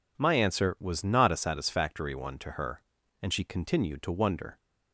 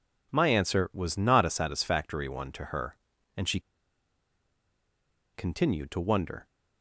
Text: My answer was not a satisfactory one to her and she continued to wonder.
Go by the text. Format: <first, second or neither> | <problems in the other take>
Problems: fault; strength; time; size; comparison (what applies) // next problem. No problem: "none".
first | pauses between "she" and "continued"; strong; at 3.5 s; 1.7 s long